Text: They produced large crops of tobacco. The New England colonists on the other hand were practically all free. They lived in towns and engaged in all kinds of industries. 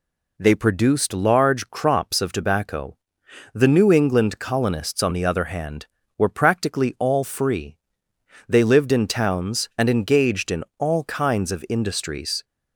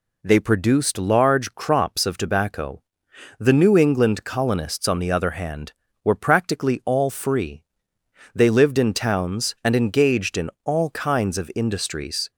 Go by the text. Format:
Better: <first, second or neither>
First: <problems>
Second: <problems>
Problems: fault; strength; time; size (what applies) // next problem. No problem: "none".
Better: neither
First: none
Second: none